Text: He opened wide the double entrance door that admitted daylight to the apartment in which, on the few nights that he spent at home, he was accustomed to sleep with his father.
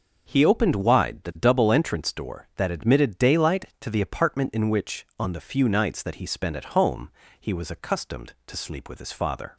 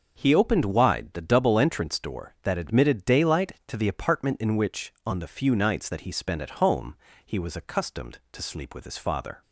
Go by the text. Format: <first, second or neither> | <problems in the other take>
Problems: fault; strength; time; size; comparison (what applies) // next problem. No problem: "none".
neither | starts louder than the rest; the same in both